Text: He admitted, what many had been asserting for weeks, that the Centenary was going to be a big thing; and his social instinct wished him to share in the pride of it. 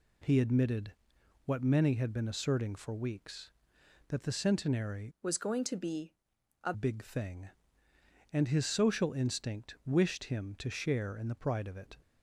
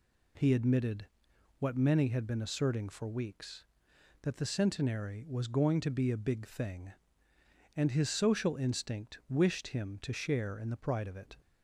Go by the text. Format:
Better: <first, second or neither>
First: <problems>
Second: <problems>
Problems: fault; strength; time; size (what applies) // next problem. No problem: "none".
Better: second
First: changes voice from "was" to "a"; from 5.2 to 6.7 s; 1.5 s long // pauses between "be" and "a"; noticeable; at 6.1 s; 0.48 s long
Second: none